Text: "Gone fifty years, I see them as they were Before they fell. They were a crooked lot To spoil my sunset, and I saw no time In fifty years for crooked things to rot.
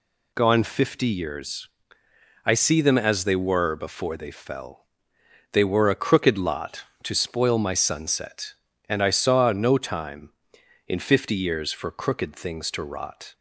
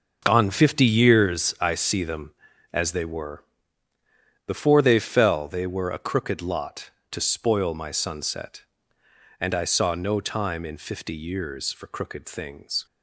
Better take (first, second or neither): first